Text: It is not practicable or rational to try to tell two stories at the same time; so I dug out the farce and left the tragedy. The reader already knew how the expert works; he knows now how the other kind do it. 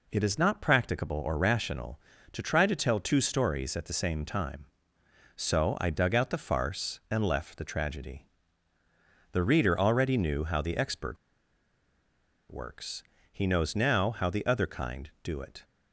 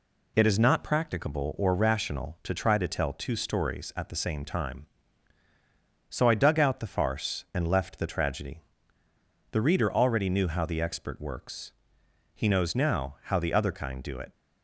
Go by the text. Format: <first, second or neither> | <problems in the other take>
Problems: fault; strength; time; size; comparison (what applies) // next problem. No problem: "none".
second | pauses between "expert" and "works"; strong; at 11.1 s; 1.3 s long